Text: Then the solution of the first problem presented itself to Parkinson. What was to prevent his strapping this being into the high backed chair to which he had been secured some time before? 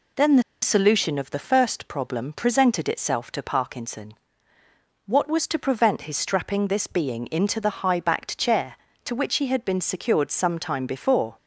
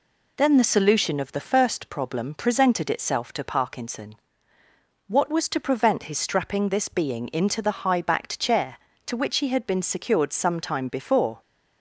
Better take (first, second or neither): second